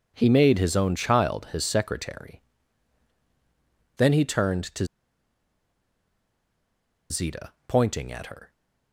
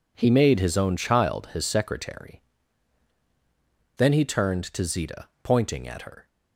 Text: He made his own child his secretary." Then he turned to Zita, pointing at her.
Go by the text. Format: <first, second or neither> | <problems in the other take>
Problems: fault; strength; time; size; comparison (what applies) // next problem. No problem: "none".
second | pauses between "to" and "Zita"; strong; at 4.8 s; 2.2 s long